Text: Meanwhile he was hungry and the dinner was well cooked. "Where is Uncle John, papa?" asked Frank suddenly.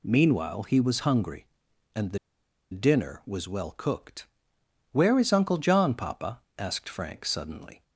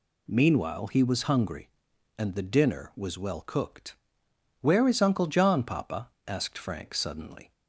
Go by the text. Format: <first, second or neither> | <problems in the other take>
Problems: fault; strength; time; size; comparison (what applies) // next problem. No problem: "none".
second | pauses between "the" and "dinner"; noticeable; at 2.1 s; 0.54 s long